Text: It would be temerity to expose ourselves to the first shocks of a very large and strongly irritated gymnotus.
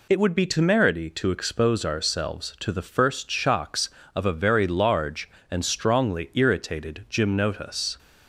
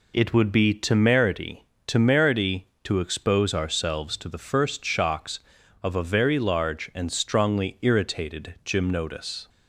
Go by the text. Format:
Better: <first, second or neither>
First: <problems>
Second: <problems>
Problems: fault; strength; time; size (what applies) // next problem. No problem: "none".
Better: first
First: none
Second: says "temerity" twice; at 1.8 s